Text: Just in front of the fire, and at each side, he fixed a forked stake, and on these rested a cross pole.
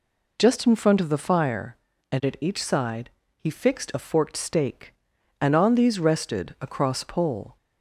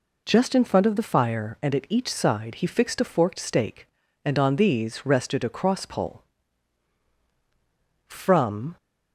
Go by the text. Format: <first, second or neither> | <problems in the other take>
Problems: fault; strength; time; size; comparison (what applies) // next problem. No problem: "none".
first | goes on to say "From"; noticeable; from 8.0 s on; 0.70 s long